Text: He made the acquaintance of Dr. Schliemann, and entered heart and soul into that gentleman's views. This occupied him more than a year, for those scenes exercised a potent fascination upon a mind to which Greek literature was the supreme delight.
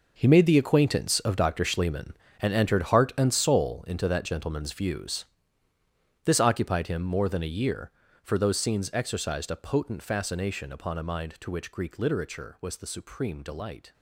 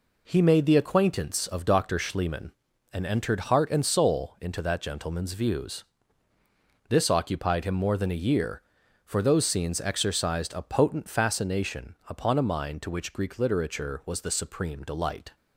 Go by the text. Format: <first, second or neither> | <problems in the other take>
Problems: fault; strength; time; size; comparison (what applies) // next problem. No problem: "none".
second | gets quieter; strong; throughout; 12 dB